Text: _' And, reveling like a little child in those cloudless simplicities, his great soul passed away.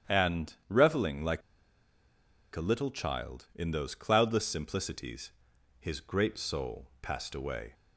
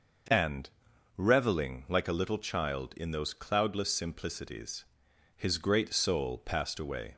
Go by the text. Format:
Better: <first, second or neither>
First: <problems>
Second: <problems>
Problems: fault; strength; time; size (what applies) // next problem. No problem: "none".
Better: second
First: starts louder than the rest; strong; until 1.2 s; 9.5 dB // pauses between "like" and "a"; at 1.4 s; 1.1 s long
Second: none